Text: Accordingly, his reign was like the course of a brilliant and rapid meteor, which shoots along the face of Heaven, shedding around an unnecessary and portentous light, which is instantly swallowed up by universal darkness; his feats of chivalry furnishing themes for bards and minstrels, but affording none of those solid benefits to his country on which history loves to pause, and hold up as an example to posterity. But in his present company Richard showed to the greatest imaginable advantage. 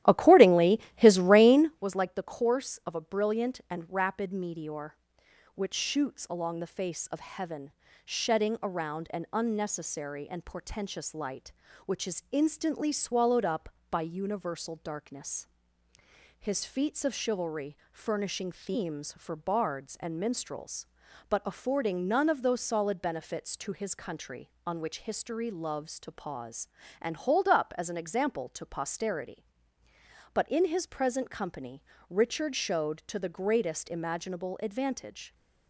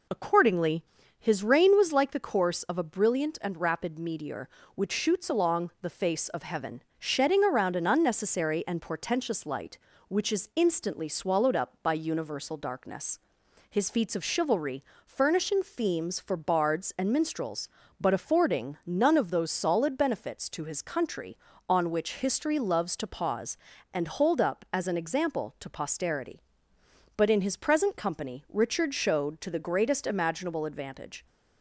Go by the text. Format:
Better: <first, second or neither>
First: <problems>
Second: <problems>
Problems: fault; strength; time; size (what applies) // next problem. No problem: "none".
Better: second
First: starts louder than the rest; strong; until 1.8 s; 13 dB // pauses between "chivalry" and "furnishing"; slight; at 17.7 s; 0.16 s long // pauses between "company" and "Richard"; slight; at 31.8 s; 0.26 s long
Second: pauses between "chivalry" and "furnishing"; slight; at 14.8 s; 0.20 s long